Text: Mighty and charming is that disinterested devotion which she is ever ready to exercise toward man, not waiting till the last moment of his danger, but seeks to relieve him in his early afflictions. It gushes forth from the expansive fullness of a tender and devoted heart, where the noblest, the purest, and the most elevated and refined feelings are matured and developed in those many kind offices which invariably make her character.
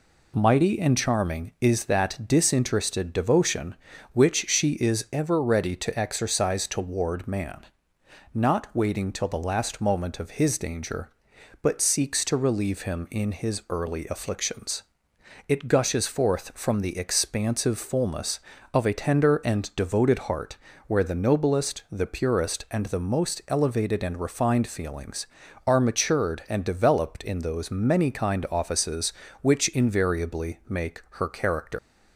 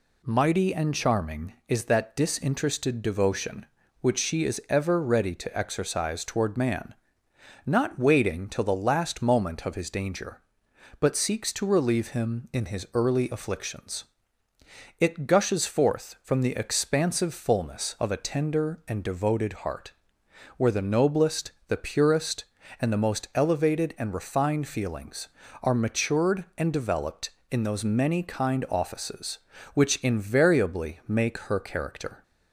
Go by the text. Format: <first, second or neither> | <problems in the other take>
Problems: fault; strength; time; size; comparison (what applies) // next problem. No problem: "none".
second | pauses between "make" and "her"; slight; at 31.0 s; 0.16 s long // leaves "character" unfinished; at 31.7 s; 160 ms